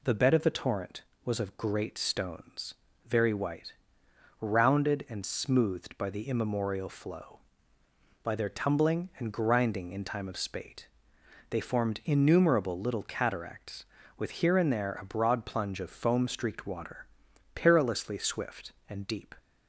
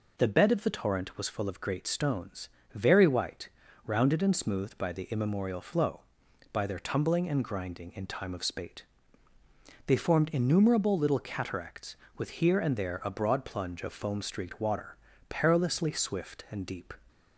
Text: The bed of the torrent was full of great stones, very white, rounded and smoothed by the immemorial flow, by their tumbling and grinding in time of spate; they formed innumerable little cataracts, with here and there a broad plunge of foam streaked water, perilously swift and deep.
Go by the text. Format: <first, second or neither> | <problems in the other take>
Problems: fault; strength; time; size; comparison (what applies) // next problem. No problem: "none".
second | skips "full"; at 1.3 s